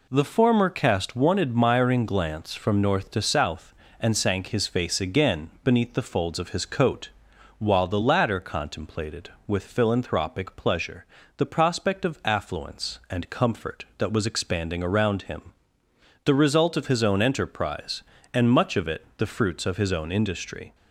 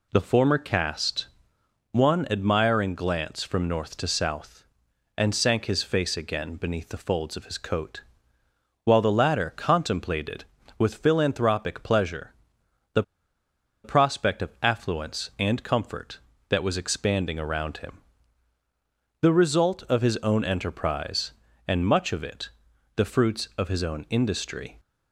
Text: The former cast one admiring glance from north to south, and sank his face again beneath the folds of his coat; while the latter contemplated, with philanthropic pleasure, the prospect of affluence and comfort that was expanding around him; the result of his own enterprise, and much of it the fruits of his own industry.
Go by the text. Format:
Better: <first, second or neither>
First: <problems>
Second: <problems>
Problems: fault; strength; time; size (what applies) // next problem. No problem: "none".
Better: first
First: none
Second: pauses between "cast" and "one"; noticeable; at 1.2 s; 0.66 s long // pauses between "the" and "prospect"; noticeable; at 13.0 s; 0.81 s long // pauses between "it" and "the"; noticeable; at 22.4 s; 0.48 s long